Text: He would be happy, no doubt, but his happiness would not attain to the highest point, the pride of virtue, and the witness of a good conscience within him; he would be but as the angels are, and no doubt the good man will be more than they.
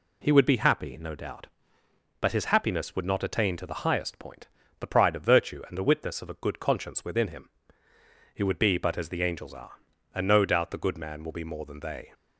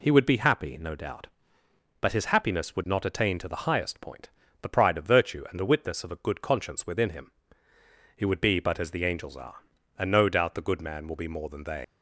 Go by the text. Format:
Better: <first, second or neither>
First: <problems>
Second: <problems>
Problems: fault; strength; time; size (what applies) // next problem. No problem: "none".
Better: first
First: none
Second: leaves "they" unfinished; at 11.8 s; 125 ms